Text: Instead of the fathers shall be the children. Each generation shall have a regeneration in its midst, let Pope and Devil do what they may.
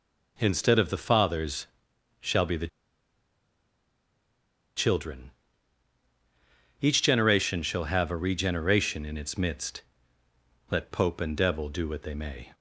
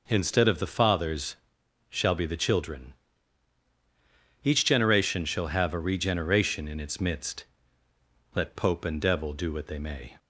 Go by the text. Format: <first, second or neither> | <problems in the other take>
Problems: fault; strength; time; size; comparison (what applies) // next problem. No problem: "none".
second | pauses between "fathers" and "shall"; noticeable; at 1.6 s; 0.56 s long; noticeable in the second // pauses between "the" and "children"; strong; at 2.6 s; 2.0 s long